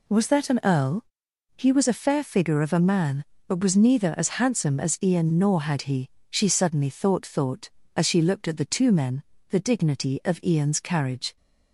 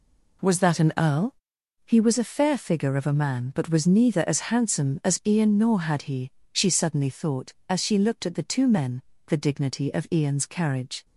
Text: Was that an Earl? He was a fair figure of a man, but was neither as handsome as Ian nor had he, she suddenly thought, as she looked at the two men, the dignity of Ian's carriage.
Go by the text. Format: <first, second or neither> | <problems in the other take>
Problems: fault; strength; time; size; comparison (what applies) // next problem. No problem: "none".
second | says "thought" twice; at 7.2 s